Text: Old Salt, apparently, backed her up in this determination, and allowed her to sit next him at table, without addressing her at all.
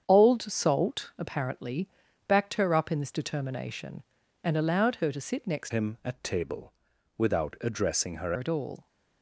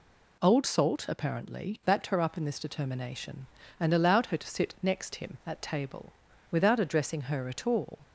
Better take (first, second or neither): second